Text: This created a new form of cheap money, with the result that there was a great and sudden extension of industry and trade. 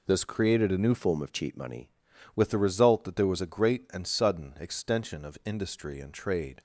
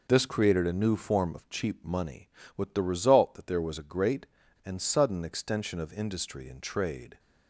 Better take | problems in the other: second | changes voice from "form" to "money"; from 0.9 to 1.9 s; 1.0 s long

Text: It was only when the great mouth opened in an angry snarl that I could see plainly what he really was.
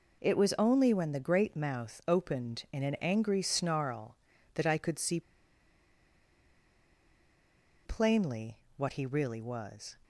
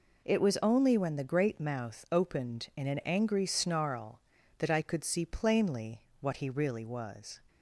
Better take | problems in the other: second | pauses between "see" and "plainly"; strong; at 5.2 s; 2.6 s long // pauses between "plainly" and "what"; slight; at 8.5 s; 0.18 s long; slight in the second

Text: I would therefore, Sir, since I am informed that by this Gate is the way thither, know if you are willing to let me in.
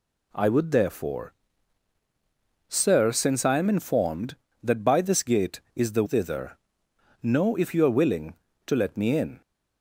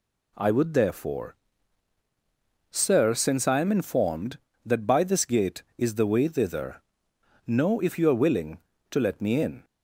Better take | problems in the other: second | skips "way"; at 6.0 s

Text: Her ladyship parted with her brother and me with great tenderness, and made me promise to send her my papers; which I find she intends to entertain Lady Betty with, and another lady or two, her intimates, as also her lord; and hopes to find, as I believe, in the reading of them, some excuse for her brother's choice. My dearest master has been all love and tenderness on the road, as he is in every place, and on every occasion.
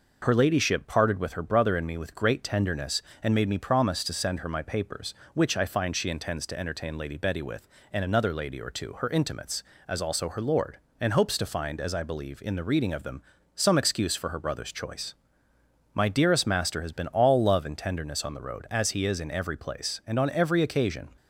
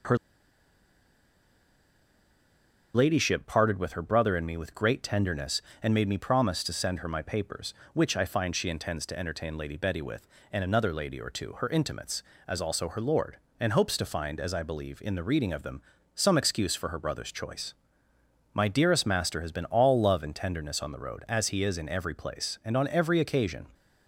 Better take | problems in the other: first | pauses between "Her" and "ladyship"; strong; at 0.1 s; 2.7 s long

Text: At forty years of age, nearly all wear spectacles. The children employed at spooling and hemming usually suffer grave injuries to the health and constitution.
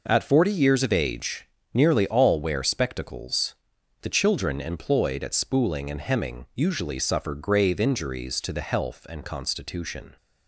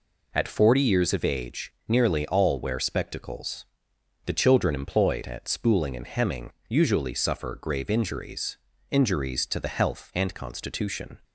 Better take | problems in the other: first | pauses between "hemming" and "usually"; slight; at 6.5 s; 0.16 s long // says "injuries" twice; at 8.9 s

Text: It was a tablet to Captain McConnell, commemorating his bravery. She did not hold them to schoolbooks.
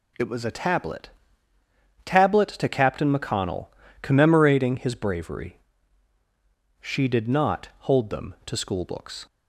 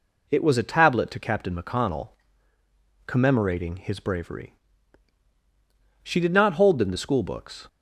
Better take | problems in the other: second | says "tablet" twice; at 2.0 s

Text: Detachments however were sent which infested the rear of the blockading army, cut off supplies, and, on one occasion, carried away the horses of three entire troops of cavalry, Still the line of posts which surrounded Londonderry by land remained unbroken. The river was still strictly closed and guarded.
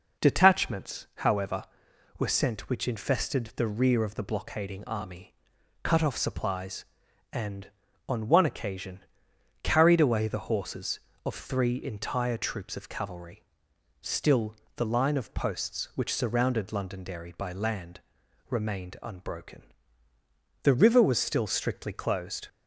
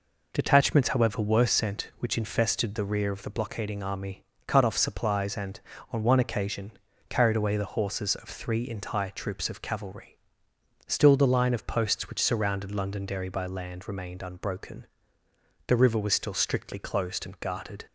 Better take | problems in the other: second | pauses between "Still" and "the"; slight; at 14.5 s; 0.22 s long // pauses between "land" and "remained"; noticeable; at 17.9 s; 0.50 s long // stops before "and guarded"; at 22.4 s

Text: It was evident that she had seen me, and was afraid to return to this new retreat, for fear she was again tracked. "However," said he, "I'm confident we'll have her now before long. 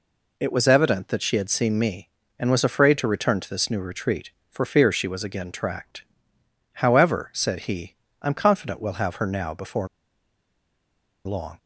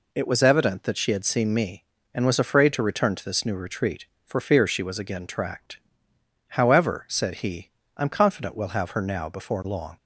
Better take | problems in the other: second | pauses between "before" and "long"; strong; at 9.8 s; 1.3 s long

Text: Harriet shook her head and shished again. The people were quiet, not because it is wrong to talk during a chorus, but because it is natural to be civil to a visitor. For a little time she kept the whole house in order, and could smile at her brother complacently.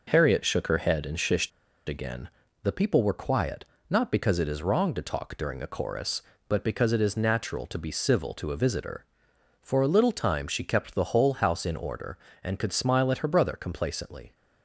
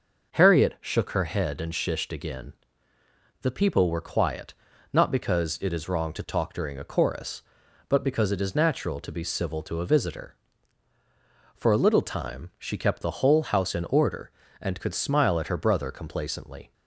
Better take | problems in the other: second | pauses between "shished" and "again"; at 1.5 s; 0.38 s long

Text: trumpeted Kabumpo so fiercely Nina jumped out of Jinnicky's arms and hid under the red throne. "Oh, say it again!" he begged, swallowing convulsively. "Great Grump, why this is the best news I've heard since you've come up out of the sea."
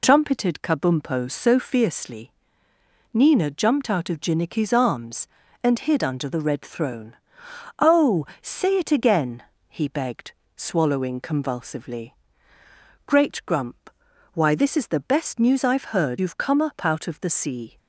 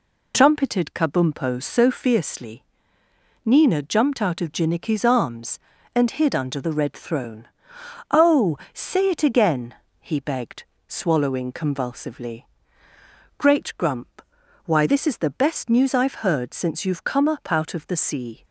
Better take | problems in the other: second | pauses between "fiercely" and "Nina"; noticeable; at 2.3 s; 0.84 s long; noticeable in the second // skips "since"; at 16.1 s

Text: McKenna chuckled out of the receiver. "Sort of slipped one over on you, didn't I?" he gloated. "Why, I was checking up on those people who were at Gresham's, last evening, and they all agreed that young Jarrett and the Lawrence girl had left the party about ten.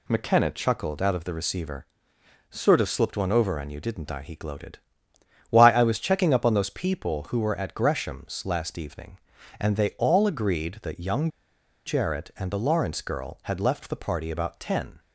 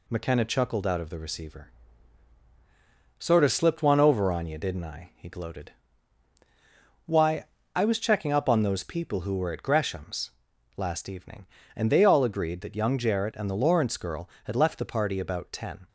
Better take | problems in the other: second | pauses between "young" and "Jarrett"; noticeable; at 11.2 s; 0.58 s long

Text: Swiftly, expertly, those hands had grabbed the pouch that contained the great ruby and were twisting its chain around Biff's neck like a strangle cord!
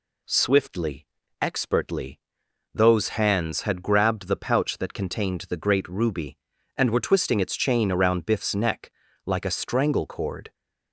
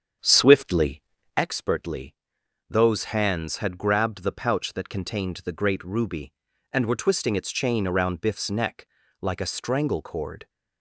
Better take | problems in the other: first | starts louder than the rest; strong; until 1.5 s; 7.5 dB // pauses between "neck" and "like"; slight; at 8.8 s; 0.36 s long; slight in the first

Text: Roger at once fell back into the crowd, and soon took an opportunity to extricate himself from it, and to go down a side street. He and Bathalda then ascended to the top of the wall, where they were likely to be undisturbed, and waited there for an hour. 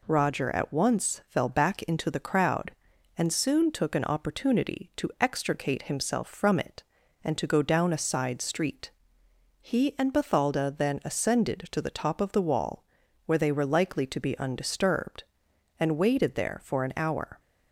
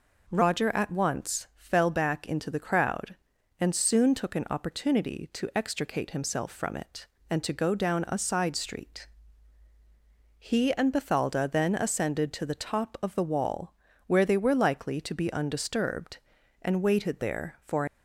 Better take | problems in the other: first | stops before "an hour"; at 17.8 s

